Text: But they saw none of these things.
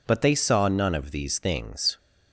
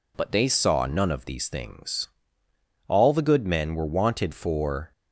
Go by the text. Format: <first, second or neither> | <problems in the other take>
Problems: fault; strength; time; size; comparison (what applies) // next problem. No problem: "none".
first | goes on to say "All the good men were wanted for"; strong; from 2.8 s on; 2.0 s long